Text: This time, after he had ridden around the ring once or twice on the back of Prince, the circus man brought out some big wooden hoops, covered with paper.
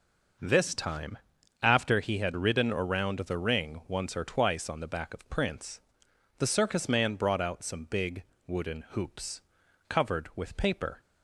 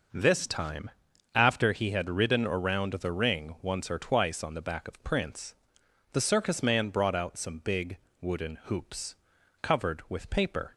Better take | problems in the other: neither | pauses between "big" and "wooden"; slight; the same in both

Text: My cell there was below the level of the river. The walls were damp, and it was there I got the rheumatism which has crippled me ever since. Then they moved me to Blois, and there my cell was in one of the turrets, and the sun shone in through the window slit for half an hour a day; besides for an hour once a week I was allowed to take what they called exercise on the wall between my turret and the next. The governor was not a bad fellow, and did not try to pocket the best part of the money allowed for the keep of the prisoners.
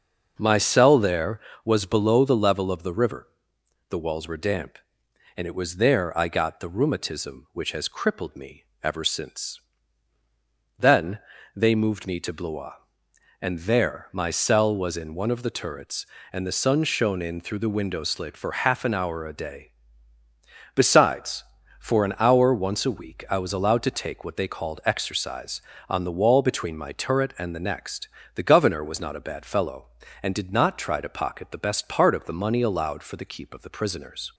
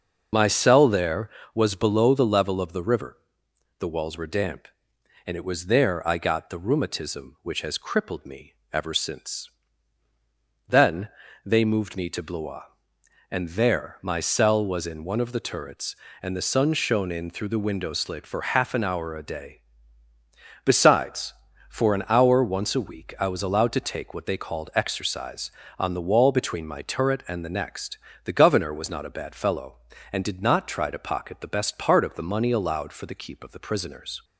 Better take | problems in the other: first | loses the start of "My"; at 0.3 s; 50 ms // starts louder than the rest; noticeable; until 1.5 s; 6 dB; also in the first // pauses between "me" and "ever"; slight; at 8.5 s; 0.18 s long; slight in the first // pauses between "Then" and "they"; slight; at 11.0 s; 0.34 s long; slight in the first

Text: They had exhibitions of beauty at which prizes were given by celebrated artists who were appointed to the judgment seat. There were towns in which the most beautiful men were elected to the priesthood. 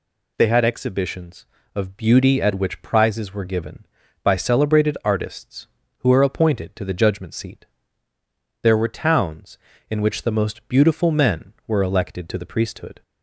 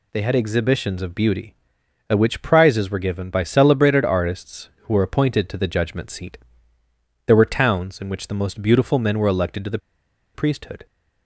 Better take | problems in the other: first | pauses between "the" and "priesthood"; noticeable; at 9.7 s; 0.56 s long

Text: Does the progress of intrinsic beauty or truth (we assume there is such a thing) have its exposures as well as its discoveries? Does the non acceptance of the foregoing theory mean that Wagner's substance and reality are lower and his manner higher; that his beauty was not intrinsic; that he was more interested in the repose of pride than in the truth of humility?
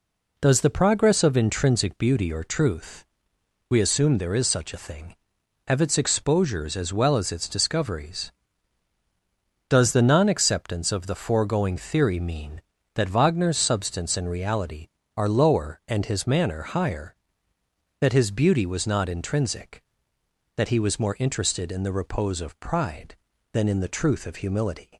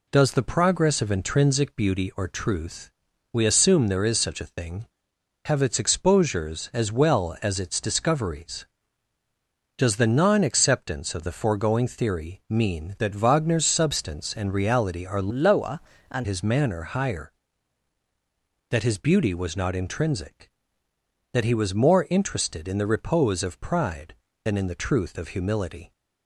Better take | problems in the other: first | changes voice from "lower" to "and"; from 15.3 to 16.2 s; 0.9 s long

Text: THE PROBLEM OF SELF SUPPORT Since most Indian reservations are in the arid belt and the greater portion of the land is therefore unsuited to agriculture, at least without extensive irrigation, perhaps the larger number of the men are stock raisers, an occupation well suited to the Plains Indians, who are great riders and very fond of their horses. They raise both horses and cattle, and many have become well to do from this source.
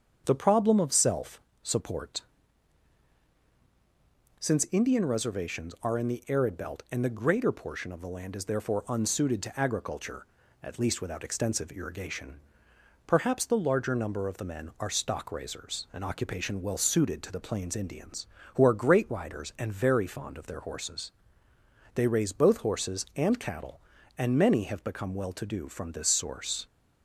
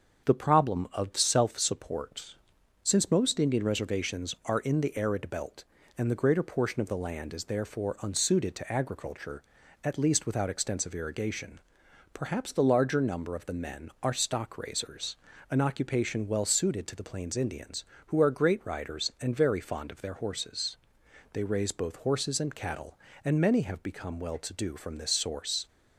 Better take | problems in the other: second | starts louder than the rest; strong; until 1.2 s; 7.5 dB; also in the second // pauses between "SELF" and "SUPPORT"; slight; at 1.3 s; 0.22 s long // pauses between "SUPPORT" and "Since"; strong; at 2.2 s; 2.1 s long; noticeable in the second // skips "most"; at 4.6 s

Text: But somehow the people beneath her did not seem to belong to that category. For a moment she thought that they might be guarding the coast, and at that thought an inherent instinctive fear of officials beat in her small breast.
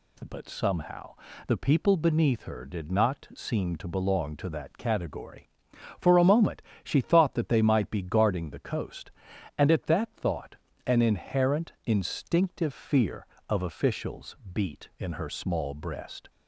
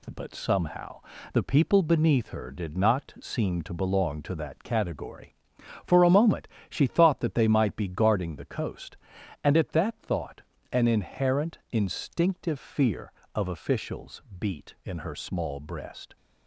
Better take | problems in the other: first | gets quieter; noticeable; throughout; 4.5 dB // pauses between "somehow" and "the"; slight; at 0.9 s; 0.32 s long; slight in the first // pauses between "moment" and "she"; slight; at 6.4 s; 0.22 s long; slight in the first // pauses between "thought" and "an"; slight; at 10.4 s; 0.32 s long; slight in the first // pauses between "officials" and "beat"; slight; at 14.2 s; 0.18 s long; slight in the first

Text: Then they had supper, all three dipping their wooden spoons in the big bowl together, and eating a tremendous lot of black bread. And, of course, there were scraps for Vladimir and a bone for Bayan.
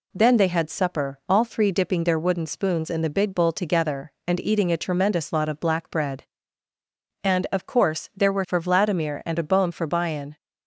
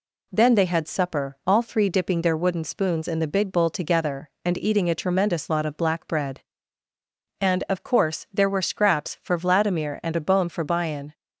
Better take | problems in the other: second | skips "scraps"; at 8.4 s

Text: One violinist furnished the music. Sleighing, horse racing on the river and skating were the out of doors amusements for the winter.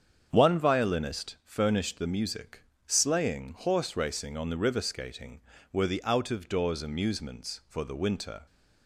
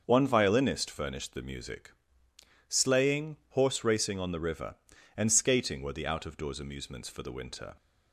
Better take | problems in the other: second | starts louder than the rest; strong; until 1.3 s; 7.5 dB; also in the second // skips "and"; at 4.7 s

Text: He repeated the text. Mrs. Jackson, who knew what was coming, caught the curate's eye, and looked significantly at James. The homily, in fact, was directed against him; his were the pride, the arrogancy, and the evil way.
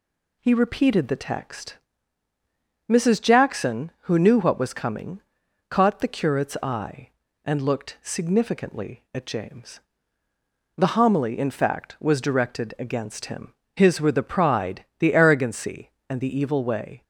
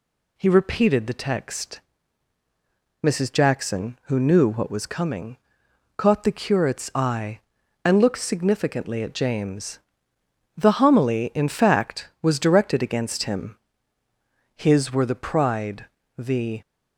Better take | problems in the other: first | stops before "arrogancy and the evil way"; at 16.6 s

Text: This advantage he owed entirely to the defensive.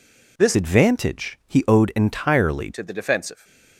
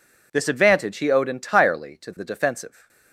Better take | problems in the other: second | changes voice from "advantage" to "entirely"; from 0.5 to 2.7 s; 2.2 s long

